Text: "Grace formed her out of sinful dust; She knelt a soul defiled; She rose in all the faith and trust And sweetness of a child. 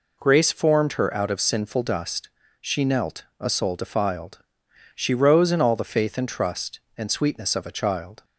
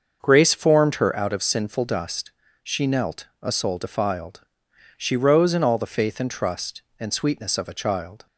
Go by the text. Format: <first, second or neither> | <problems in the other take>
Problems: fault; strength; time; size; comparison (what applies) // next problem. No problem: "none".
first | starts louder than the rest; until 1.2 s; 6.5 dB